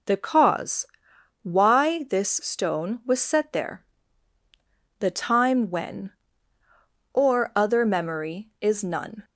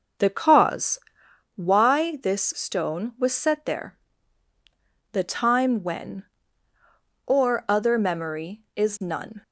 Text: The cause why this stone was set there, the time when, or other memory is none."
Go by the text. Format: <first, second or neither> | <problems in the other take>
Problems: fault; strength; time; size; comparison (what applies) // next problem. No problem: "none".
first | starts louder than the rest; noticeable; until 1.3 s; 6 dB // pauses between "cause" and "why"; noticeable; at 0.9 s; 0.58 s long; noticeable in the first